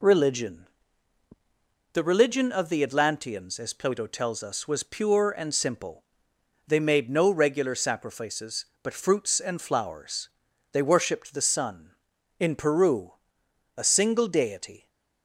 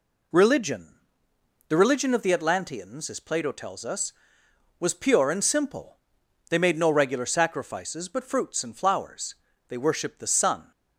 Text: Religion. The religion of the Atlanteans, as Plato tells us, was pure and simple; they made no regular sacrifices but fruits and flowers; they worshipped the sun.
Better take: second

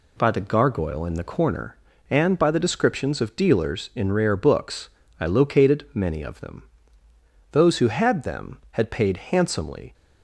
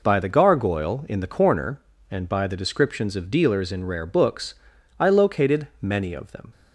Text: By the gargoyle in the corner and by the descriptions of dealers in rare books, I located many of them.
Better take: second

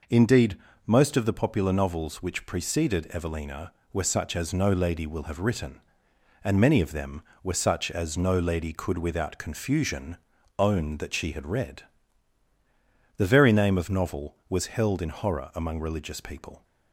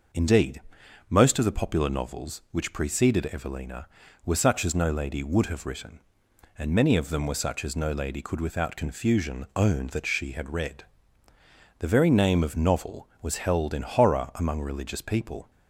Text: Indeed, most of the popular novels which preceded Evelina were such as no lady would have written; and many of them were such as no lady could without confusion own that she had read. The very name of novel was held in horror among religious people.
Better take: second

